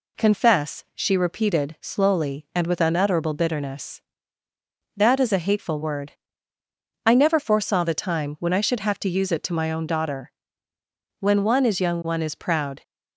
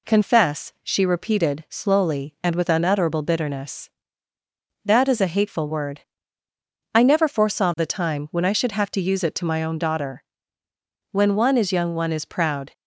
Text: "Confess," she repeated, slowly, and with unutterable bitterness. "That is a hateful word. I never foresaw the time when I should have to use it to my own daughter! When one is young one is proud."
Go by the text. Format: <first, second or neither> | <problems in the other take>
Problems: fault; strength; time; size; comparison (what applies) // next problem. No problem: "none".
neither | none